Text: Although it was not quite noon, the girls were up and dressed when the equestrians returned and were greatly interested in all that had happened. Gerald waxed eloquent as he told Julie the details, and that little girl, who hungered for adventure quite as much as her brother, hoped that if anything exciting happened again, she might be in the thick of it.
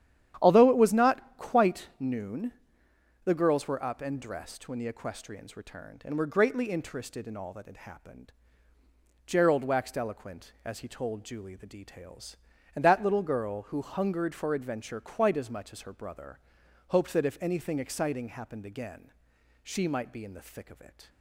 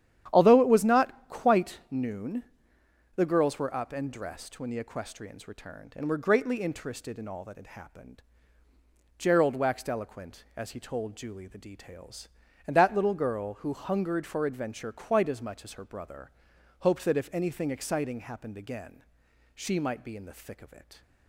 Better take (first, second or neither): neither